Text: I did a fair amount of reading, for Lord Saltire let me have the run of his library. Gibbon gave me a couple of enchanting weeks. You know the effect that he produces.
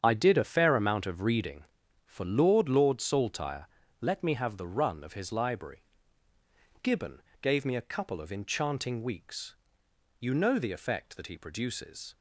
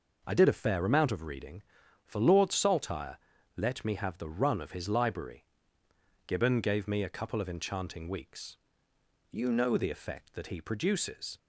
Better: second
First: starts louder than the rest; strong; until 1.0 s; 8 dB // says "Lord" twice; at 2.7 s // pauses between "Saltire" and "let"; slight; at 3.6 s; 0.34 s long // pauses between "Gibbon" and "gave"; slight; at 7.2 s; 0.22 s long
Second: pauses between "Saltire" and "let"; at 3.1 s; 0.40 s long

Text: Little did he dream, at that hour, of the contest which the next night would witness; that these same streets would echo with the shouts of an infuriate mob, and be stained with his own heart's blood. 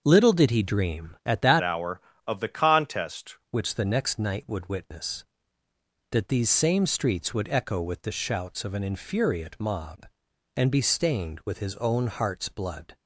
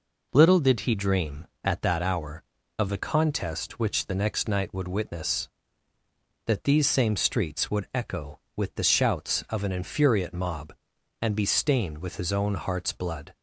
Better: second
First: starts louder than the rest; until 1.0 s; 6.5 dB // changes voice from "hour" to "contest"; from 1.6 to 3.3 s; 1.7 s long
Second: none

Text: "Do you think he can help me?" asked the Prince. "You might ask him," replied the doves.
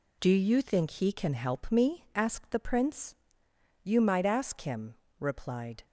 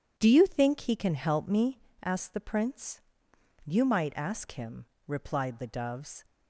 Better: second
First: stops before "the doves"; at 5.8 s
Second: none

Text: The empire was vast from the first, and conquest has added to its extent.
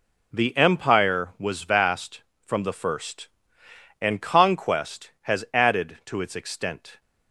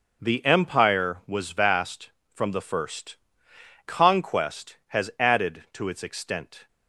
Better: first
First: none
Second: skips "and"; at 3.5 s

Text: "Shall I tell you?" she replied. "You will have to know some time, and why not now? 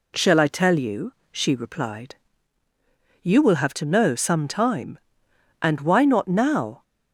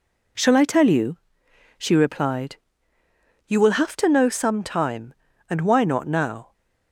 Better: neither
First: none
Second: none

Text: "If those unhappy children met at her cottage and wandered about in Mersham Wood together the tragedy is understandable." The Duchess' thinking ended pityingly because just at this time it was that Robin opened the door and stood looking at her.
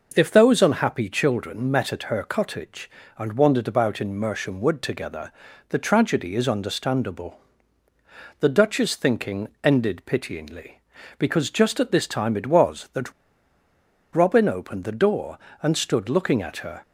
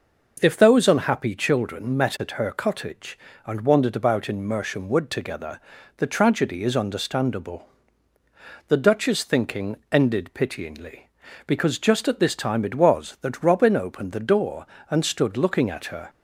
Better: second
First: pauses between "together" and "the"; at 5.3 s; 0.38 s long // pauses between "thinking" and "ended"; slight; at 9.4 s; 0.16 s long // pauses between "that" and "Robin"; at 13.1 s; 1.0 s long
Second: pauses between "together" and "the"; at 5.6 s; 0.38 s long // pauses between "thinking" and "ended"; slight; at 9.7 s; 0.16 s long

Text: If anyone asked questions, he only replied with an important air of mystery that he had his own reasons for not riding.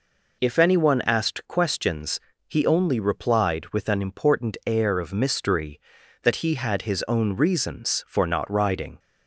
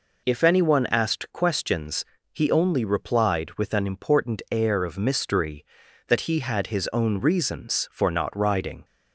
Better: neither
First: none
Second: none

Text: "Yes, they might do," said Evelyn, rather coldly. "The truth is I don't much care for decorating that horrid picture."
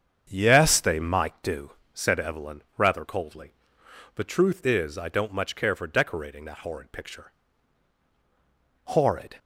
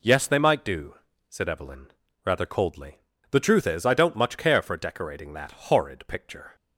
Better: second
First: starts louder than the rest; strong; until 1.3 s; 7.5 dB // goes on to say "Horrid"; from 8.8 s on; 0.54 s long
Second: none

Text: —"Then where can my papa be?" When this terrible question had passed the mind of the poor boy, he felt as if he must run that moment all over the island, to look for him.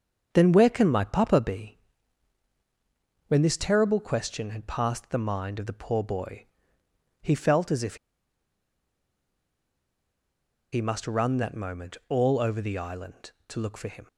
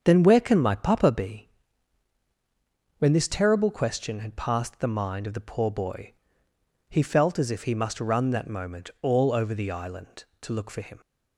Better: second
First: starts louder than the rest; until 1.3 s; 6.5 dB // pauses between "if" and "he"; strong; at 7.9 s; 2.7 s long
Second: starts louder than the rest; until 1.0 s; 6.5 dB

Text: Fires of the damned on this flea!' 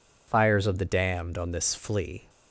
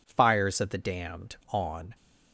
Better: first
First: none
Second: stops before "this flea"; at 1.9 s

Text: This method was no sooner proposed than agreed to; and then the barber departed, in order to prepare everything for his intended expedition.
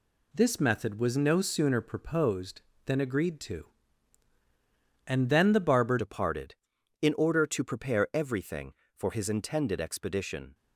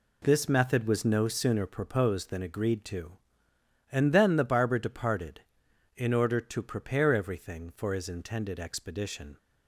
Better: second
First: changes voice at "departed"; from 5.9 s on; 4.6 s long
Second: none

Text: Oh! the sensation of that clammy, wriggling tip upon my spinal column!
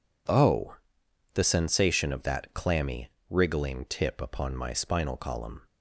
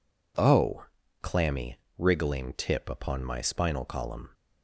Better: first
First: none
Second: skips "the sensation of that"; at 1.0 s

